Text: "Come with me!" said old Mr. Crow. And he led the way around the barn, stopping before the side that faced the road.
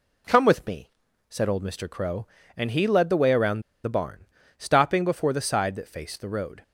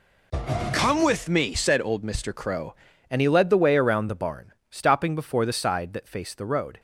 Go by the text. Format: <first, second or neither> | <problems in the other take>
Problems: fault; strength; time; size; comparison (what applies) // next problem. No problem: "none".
second | pauses between "around" and "the"; slight; at 3.6 s; 0.23 s long